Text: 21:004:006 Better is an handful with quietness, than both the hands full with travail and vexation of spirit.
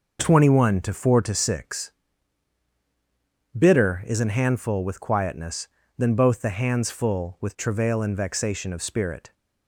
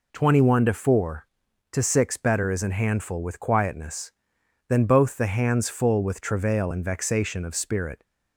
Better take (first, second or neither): second